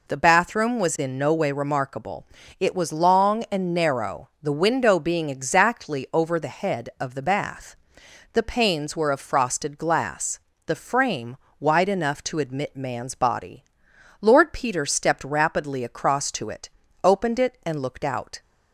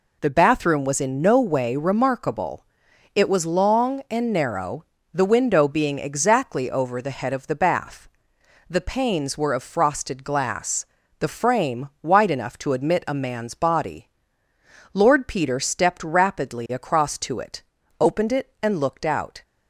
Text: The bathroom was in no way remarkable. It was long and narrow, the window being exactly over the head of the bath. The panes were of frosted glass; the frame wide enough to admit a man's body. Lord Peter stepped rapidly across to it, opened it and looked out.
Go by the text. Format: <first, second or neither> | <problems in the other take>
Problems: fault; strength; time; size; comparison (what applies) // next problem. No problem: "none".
second | pauses between "frame" and "wide"; slight; at 11.3 s; 0.24 s long; slight in the second // skips "a"; at 12.7 s